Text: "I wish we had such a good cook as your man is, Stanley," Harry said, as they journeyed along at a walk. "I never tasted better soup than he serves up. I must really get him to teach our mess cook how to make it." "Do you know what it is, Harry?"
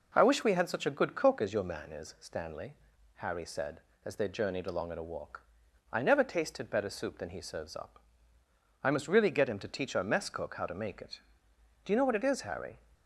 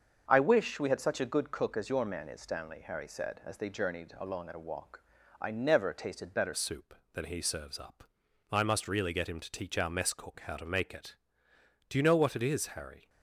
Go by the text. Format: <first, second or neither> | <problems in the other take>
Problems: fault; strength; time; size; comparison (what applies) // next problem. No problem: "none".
first | starts louder than the rest; until 1.2 s; 6.5 dB // changes voice at "soup"; from 6.5 s on; 6.5 s long